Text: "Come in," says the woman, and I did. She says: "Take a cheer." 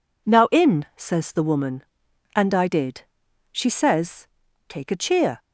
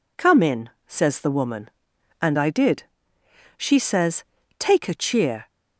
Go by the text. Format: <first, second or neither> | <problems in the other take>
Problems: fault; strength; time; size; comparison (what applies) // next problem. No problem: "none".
second | says "Now" for "Come"; at 0.2 s